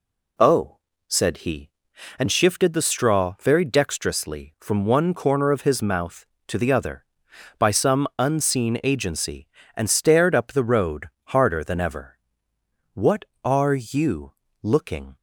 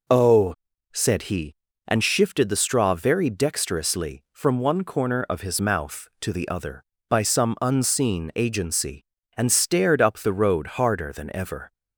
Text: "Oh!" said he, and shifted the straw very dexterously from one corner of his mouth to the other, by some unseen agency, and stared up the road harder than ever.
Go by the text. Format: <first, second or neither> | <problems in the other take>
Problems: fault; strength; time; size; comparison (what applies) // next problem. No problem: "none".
second | pauses between "road" and "harder"; slight; at 11.0 s; 0.16 s long // goes on to say "What are you looking"; strong; from 12.9 s on; 2.2 s long